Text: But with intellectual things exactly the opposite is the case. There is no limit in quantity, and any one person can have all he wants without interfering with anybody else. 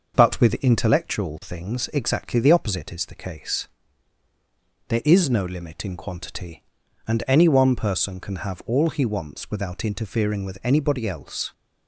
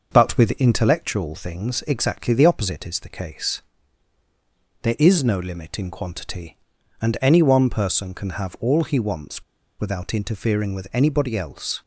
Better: first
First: starts louder than the rest; noticeable; until 1.1 s; 6 dB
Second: starts louder than the rest; noticeable; until 1.1 s; 6 dB // pauses between "wants" and "without"; at 9.4 s; 0.36 s long

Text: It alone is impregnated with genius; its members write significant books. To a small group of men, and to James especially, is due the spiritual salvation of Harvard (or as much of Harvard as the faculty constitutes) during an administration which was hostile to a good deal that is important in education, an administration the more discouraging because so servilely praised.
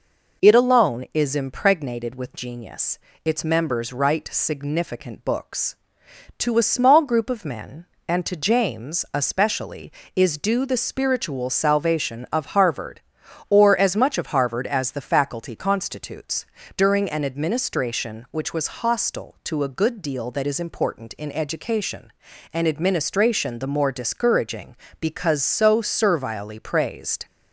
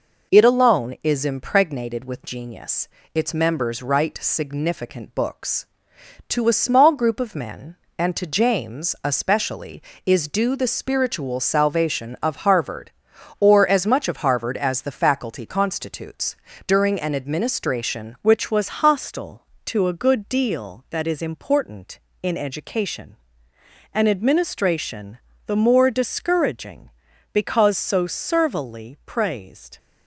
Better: first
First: none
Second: changes voice at "which"; from 18.2 s on; 11.5 s long // pauses between "administration" and "the"; slight; at 25.1 s; 0.28 s long

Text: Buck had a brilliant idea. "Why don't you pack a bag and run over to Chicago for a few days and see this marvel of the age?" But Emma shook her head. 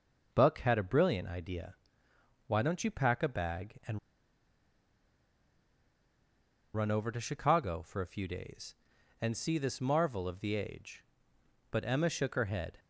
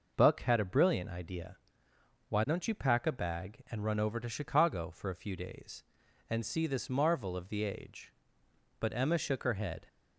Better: second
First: pauses between "and" and "run"; strong; at 3.9 s; 2.7 s long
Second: none

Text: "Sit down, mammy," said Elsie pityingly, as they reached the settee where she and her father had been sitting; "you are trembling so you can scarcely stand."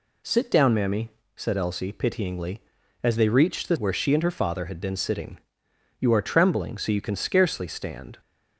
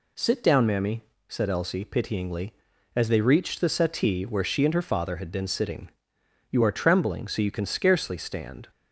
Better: second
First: skips "settee"; at 3.7 s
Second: none

